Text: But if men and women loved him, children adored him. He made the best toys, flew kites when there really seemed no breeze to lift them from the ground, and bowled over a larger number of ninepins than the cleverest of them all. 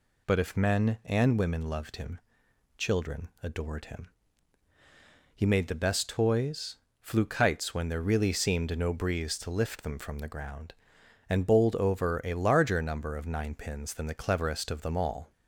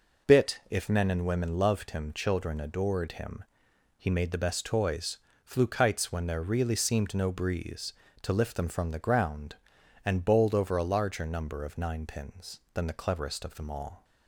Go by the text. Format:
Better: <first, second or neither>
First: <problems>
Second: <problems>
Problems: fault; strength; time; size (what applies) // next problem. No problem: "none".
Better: first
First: none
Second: says "Bit" for "But"; at 0.2 s